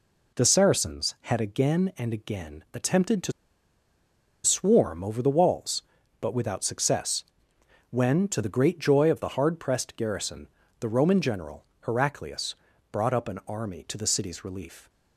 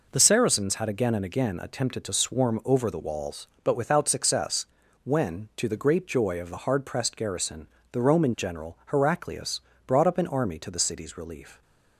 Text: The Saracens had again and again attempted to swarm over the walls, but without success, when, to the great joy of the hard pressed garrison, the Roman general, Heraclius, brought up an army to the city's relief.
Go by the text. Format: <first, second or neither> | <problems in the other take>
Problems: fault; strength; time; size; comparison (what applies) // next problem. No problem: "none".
second | pauses between "to" and "swarm"; at 3.3 s; 1.1 s long